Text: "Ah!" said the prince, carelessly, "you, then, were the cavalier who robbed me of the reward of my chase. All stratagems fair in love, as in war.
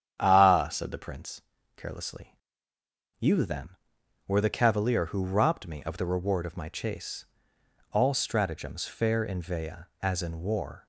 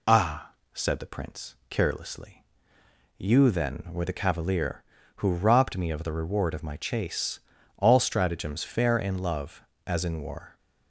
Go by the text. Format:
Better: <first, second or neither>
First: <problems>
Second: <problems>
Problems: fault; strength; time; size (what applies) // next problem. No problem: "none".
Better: second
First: starts louder than the rest; strong; until 1.2 s; 9 dB // says "vea" for "love"; at 9.3 s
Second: none